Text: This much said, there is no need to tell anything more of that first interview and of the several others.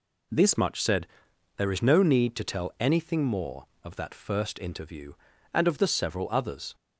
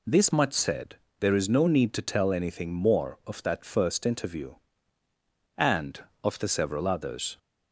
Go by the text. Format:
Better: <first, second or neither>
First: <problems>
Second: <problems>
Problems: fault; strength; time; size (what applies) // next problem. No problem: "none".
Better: second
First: changes voice at "much"; from 0.5 s on; 6.2 s long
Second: none